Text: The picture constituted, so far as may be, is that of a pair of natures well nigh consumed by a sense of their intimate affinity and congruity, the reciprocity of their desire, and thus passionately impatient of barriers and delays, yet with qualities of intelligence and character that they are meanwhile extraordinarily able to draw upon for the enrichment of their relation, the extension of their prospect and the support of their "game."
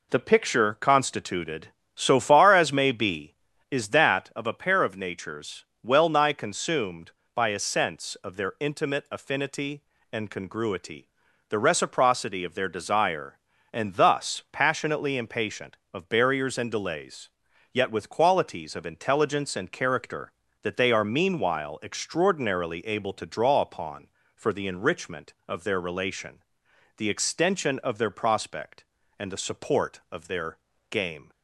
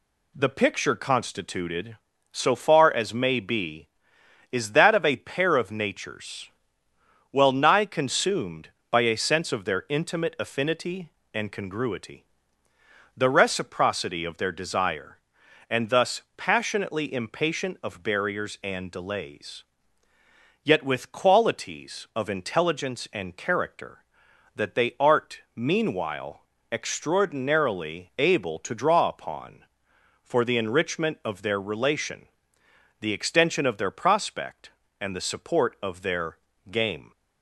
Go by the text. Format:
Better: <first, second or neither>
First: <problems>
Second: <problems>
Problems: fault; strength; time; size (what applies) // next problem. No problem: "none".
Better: first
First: pauses between "natures" and "well"; slight; at 5.6 s; 0.20 s long // pauses between "their" and "game"; slight; at 30.5 s; 0.34 s long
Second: pauses between "natures" and "well"; noticeable; at 6.4 s; 0.86 s long // says "art" for "are"; at 24.9 s // pauses between "meanwhile" and "extraordinarily"; slight; at 26.4 s; 0.30 s long // pauses between "their" and "game"; slight; at 36.3 s; 0.34 s long